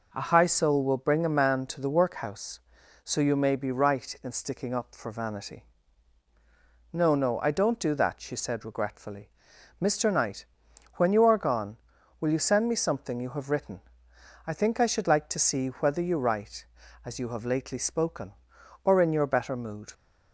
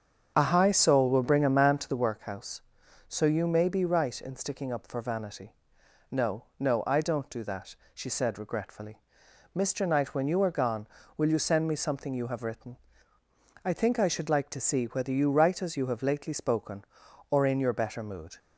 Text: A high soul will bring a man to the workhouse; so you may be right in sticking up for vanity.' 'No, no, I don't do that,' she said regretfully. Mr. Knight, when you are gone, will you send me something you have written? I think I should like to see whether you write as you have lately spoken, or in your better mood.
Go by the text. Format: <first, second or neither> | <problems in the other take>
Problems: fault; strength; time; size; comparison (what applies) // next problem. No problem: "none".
first | starts louder than the rest; strong; until 2.2 s; 7.5 dB